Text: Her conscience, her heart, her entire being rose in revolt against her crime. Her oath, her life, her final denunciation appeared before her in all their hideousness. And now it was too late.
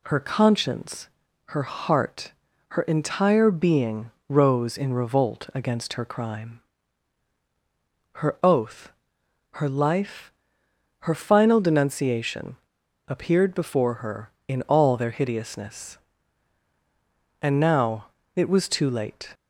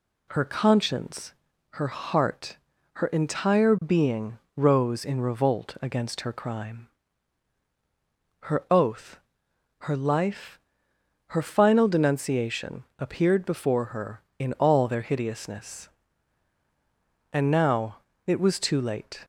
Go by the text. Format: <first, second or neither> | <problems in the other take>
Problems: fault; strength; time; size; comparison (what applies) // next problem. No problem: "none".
second | pauses between "being" and "rose"; slight; at 4.1 s; 0.16 s long; slight in the second // pauses between "denunciation" and "appeared"; noticeable; at 12.5 s; 0.50 s long // pauses between "now" and "it"; slight; at 18.0 s; 0.28 s long; slight in the second